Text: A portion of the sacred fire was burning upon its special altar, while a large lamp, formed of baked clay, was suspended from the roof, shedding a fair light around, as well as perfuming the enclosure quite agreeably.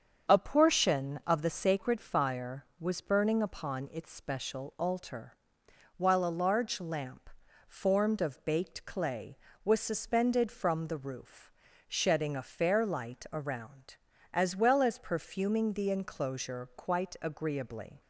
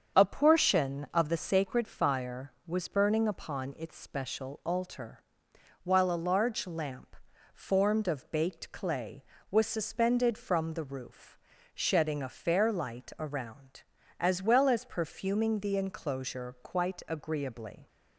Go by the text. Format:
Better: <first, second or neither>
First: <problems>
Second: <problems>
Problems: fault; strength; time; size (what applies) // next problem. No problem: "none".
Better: neither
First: starts louder than the rest; strong; until 1.3 s; 7 dB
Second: starts louder than the rest; strong; until 1.2 s; 7 dB